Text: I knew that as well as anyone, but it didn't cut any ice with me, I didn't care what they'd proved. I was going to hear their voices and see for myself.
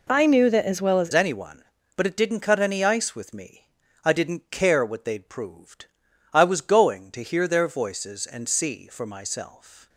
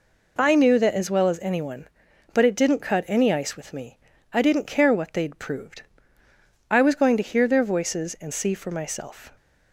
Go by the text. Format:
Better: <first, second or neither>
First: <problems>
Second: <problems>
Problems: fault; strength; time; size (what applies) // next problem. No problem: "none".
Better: second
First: changes voice at "anyone"; from 1.1 s on; 8.7 s long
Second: none